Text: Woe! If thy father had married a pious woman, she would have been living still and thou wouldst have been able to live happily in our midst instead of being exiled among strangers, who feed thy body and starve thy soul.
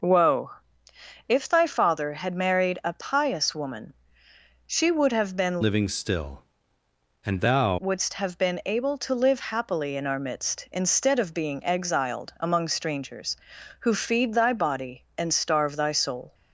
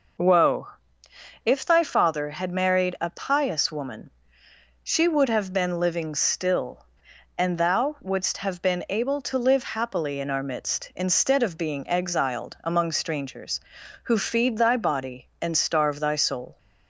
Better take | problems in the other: second | changes voice from "living" to "thou"; from 5.6 to 7.7 s; 2.1 s long

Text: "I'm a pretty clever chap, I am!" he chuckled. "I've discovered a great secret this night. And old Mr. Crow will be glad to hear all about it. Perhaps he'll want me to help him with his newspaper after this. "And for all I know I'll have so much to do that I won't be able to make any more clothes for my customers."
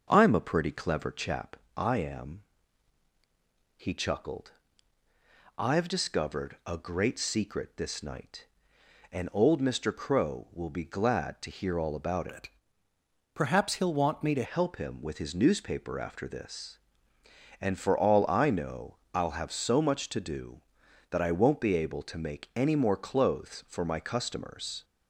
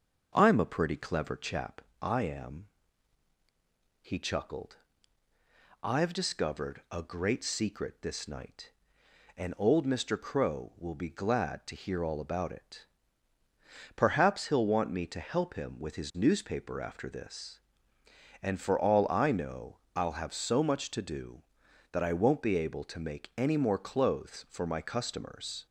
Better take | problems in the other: second | starts louder than the rest; until 1.1 s; 6.5 dB; also in the second // changes voice from "it" to "to"; from 12.3 to 14.4 s; 2.1 s long // pauses between "know" and "I'll"; slight; at 18.9 s; 0.16 s long; slight in the second

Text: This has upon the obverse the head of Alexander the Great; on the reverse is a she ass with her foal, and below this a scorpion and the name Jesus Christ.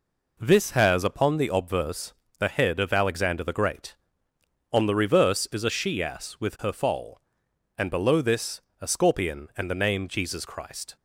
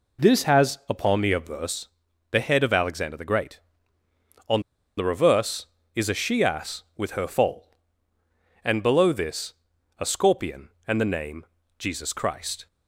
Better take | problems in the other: first | pauses between "obverse" and "the"; at 1.8 s; 0.44 s long; slight in the first // pauses between "on" and "the"; at 4.5 s; 0.37 s long // pauses between "this" and "a"; noticeable; at 9.5 s; 0.46 s long; slight in the first // pauses between "name" and "Jesus"; slight; at 11.4 s; 0.32 s long

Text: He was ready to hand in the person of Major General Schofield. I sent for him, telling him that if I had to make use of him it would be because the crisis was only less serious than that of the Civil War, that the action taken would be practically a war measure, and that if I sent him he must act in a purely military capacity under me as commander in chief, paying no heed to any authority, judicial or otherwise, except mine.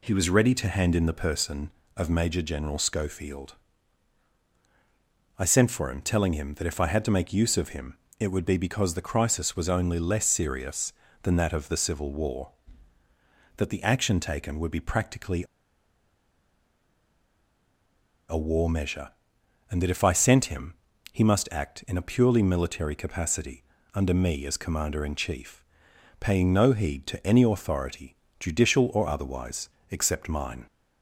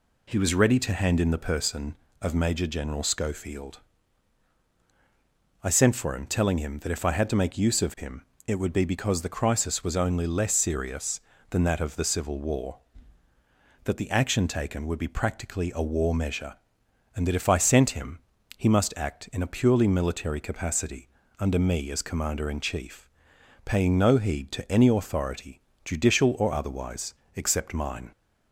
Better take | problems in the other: second | pauses between "him" and "it"; slight; at 7.9 s; 0.26 s long; slight in the second // pauses between "practically" and "a"; strong; at 15.4 s; 2.8 s long // pauses between "him" and "he"; slight; at 20.7 s; 0.36 s long; slight in the second // pauses between "capacity" and "under"; slight; at 23.6 s; 0.30 s long; slight in the second

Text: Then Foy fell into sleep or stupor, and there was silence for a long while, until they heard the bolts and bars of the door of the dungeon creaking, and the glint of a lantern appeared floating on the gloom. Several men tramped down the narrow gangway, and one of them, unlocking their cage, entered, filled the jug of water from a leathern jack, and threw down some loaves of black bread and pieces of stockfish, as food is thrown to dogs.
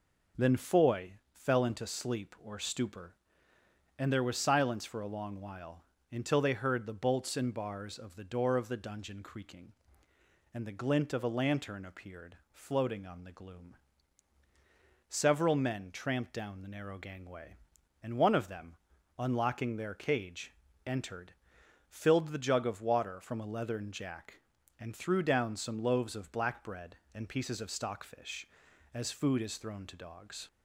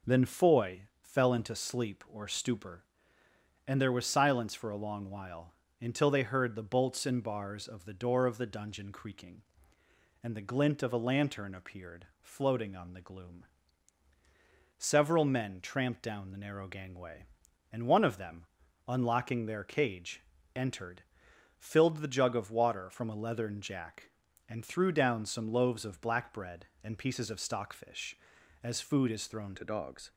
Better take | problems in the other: first | pauses between "Foy" and "fell"; slight; at 0.8 s; 0.18 s long; slight in the first // pauses between "appeared" and "floating"; slight; at 12.0 s; 0.16 s long; slight in the first // changes voice at "to"; from 29.5 s on; 0.6 s long

